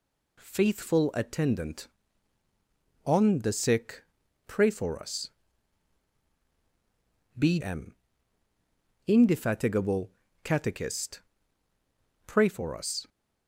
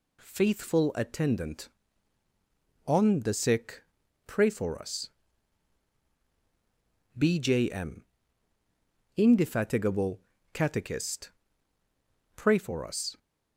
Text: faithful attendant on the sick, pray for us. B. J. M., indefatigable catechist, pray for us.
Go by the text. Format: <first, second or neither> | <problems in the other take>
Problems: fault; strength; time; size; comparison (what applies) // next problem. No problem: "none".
second | skips "J"; at 7.5 s // pauses between "indefatigable" and "catechist"; slight; at 10.1 s; 0.32 s long; slight in the second